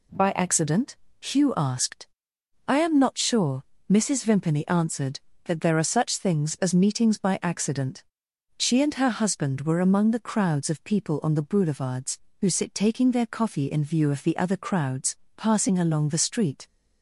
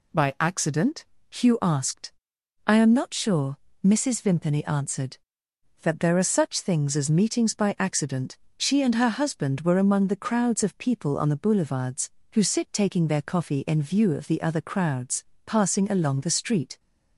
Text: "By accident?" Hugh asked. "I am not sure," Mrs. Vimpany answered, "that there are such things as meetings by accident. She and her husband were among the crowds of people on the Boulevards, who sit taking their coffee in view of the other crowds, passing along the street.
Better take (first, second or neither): neither